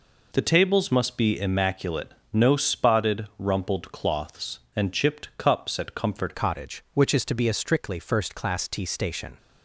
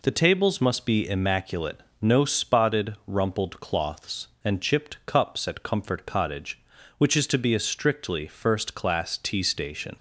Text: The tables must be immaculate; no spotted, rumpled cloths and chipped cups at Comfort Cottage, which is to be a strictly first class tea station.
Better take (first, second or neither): second